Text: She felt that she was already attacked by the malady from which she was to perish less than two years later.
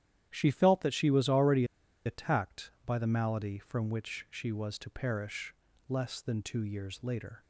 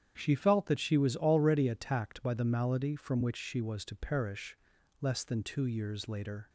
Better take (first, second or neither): second